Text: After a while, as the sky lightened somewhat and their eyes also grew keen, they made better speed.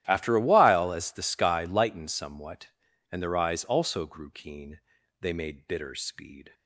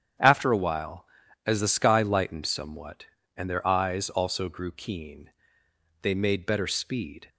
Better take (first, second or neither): second